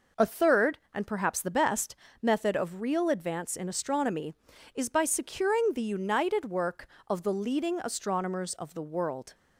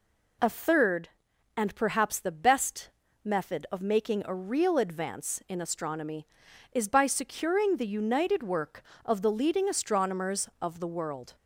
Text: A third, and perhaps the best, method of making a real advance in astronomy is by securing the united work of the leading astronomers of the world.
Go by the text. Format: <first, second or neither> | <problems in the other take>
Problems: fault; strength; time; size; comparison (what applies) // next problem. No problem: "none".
second | skips "making a"; at 2.8 s